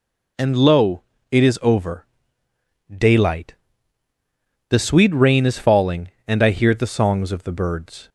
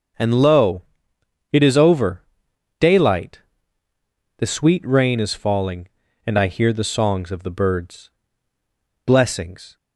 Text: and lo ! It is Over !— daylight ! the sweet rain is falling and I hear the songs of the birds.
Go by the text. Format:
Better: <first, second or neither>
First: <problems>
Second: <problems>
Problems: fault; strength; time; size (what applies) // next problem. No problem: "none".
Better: first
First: none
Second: goes on to say "Blessings"; noticeable; from 9.0 s on; 0.72 s long